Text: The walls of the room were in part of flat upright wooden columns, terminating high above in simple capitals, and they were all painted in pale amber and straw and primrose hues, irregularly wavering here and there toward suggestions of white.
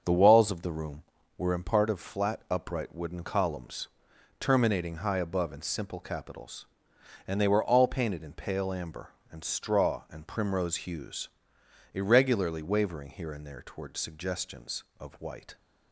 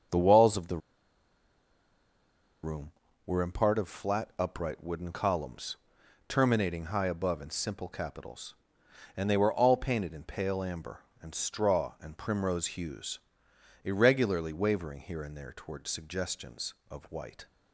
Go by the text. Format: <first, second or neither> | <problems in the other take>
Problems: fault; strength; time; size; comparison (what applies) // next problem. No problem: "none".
first | starts louder than the rest; until 3.3 s; 7 dB; also in the first // pauses between "the" and "room"; strong; at 0.7 s; 1.8 s long